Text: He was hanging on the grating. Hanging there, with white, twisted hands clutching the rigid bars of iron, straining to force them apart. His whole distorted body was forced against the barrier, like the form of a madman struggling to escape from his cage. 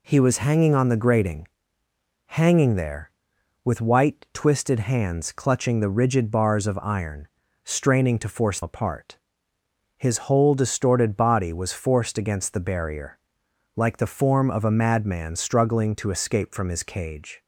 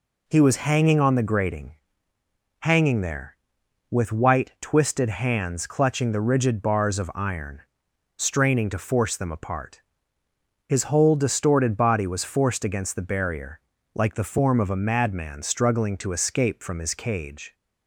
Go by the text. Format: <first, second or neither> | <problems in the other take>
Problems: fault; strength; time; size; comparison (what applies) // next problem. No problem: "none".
second | skips "them"; at 8.6 s